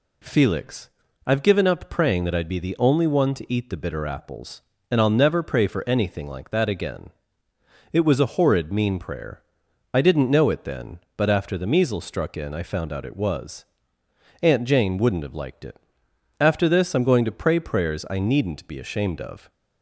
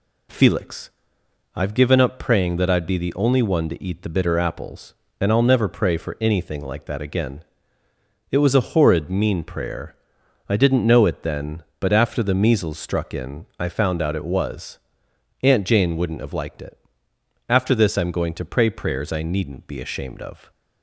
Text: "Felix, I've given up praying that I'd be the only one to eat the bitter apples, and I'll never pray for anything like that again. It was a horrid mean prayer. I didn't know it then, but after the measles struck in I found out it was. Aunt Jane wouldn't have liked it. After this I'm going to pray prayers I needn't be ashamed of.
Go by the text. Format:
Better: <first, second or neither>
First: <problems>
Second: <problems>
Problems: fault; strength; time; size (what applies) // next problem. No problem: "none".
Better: neither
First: none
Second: none